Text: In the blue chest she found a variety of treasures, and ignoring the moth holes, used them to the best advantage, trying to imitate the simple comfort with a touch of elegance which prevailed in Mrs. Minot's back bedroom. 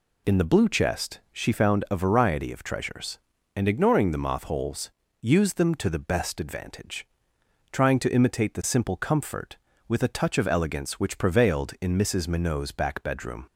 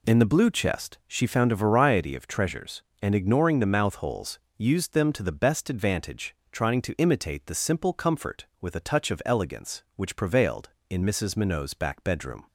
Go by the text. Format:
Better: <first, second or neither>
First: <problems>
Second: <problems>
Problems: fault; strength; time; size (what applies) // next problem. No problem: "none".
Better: first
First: none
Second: says "mouth" for "moth"; at 3.7 s